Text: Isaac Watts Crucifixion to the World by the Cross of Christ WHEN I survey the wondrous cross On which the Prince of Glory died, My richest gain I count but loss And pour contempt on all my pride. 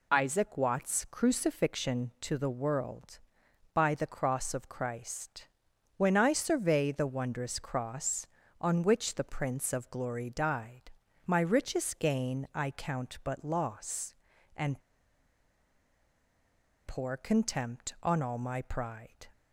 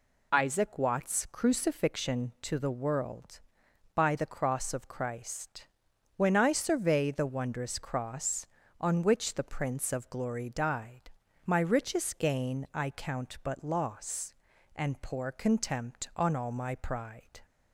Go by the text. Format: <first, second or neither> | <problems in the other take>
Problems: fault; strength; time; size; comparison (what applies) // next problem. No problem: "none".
second | pauses between "Christ" and "WHEN"; noticeable; at 5.4 s; 0.50 s long; noticeable in the second // pauses between "And" and "pour"; strong; at 14.7 s; 2.0 s long